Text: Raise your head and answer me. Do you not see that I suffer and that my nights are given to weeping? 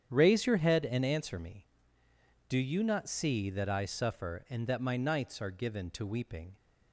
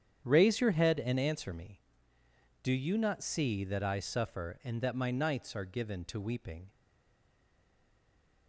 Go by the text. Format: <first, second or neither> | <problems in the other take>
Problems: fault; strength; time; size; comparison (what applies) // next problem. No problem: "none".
first | starts louder than the rest; strong; until 1.2 s; 8.5 dB; strong in the first // stays silent after the last word; noticeable; from 6.7 s on; 1.7 s long